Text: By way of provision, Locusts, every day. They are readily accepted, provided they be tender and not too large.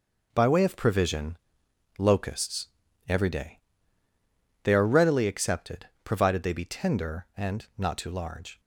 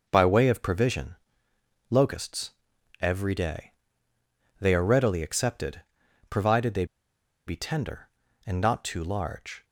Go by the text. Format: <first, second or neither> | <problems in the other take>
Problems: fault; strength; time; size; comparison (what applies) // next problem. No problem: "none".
first | pauses between "they" and "be"; noticeable; at 6.8 s; 0.61 s long